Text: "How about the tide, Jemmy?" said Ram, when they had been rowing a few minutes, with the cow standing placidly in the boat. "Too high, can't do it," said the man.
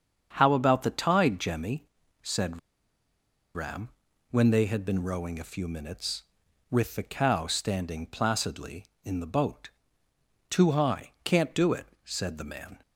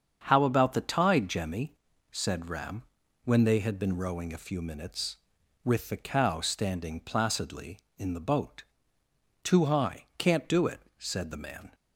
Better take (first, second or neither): second